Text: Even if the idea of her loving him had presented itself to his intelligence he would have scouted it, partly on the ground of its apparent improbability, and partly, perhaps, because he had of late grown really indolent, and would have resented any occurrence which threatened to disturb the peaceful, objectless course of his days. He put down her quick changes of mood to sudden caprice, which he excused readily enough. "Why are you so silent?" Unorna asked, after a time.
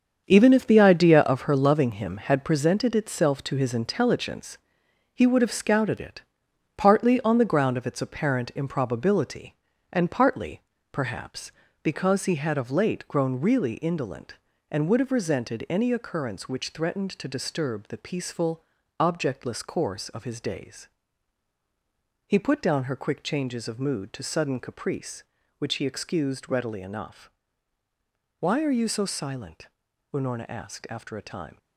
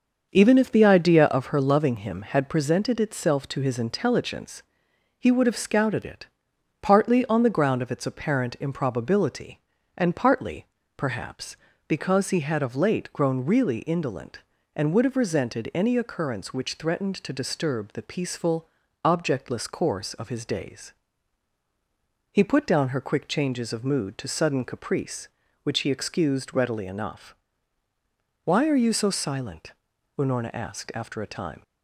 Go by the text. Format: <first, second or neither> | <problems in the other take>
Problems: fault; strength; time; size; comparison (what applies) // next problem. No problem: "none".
second | gets quieter; strong; throughout; 9.5 dB // starts louder than the rest; until 1.2 s; 7 dB; also in the second // pauses between "intelligence" and "he"; noticeable; at 4.5 s; 0.58 s long; noticeable in the second